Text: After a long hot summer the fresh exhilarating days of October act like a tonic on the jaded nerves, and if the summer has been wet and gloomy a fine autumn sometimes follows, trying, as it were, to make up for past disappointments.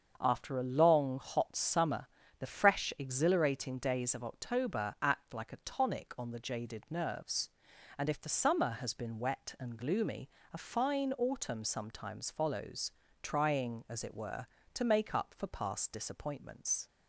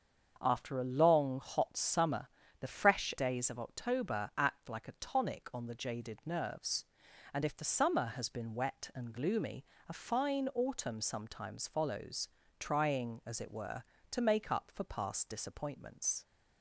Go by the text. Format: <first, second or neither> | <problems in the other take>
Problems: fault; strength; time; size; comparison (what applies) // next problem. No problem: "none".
first | starts louder than the rest; until 1.4 s; 6.5 dB; also in the first // pauses between "summer" and "the"; slight; at 2.2 s; 0.32 s long; slight in the first // skips "exhilarating"; at 3.1 s // pauses between "gloomy" and "a"; slight; at 9.6 s; 0.24 s long; slight in the first